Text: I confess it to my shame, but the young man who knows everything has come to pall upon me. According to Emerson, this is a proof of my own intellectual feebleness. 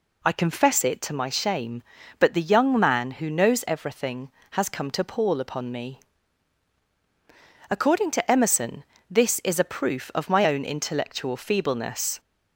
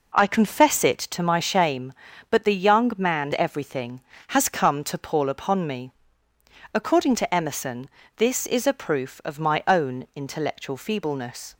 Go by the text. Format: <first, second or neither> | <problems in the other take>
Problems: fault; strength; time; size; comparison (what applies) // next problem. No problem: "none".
first | skips "who knows"; at 3.3 s